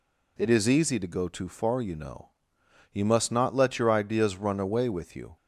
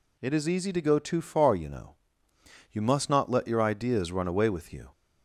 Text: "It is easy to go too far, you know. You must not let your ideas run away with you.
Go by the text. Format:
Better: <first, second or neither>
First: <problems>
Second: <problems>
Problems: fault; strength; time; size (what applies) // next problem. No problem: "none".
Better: neither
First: none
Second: none